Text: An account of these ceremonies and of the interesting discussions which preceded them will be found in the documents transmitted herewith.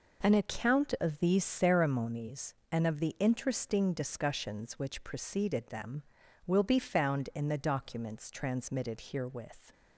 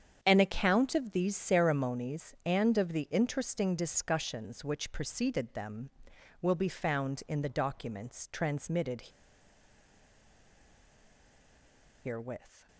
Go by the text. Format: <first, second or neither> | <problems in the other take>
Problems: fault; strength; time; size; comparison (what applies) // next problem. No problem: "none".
first | starts louder than the rest; strong; until 1.2 s; 8 dB // pauses between "transmitted" and "herewith"; strong; at 9.0 s; 3.0 s long